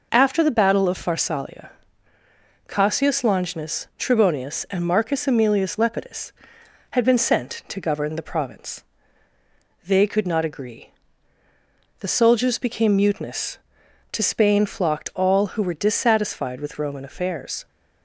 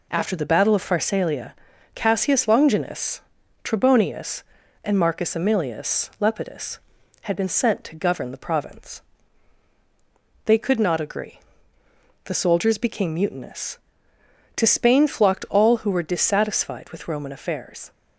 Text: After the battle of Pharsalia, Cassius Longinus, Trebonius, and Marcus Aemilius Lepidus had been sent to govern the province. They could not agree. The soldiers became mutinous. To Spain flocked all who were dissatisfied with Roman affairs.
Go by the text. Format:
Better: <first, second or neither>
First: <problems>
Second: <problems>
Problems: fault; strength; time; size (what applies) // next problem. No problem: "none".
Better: neither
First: none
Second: none